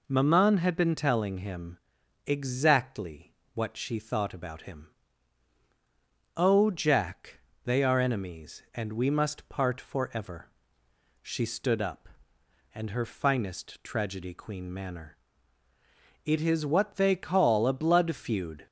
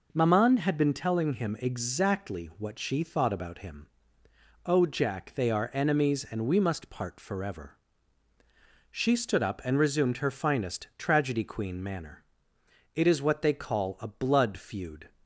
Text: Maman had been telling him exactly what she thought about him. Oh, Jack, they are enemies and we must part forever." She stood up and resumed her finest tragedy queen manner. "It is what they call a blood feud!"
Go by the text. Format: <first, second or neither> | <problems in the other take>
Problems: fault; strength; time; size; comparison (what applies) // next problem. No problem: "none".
second | pauses between "him" and "exactly"; noticeable; at 1.7 s; 0.48 s long // pauses between "exactly" and "what"; slight; at 3.3 s; 0.22 s long // skips "resumed"; at 12.9 s